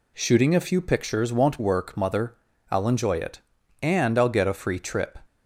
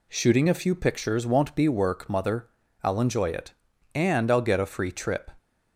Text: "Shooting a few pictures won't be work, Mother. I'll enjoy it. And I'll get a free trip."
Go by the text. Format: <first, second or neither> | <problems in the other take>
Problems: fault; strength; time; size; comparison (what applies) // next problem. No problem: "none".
second | skips "be"; at 1.5 s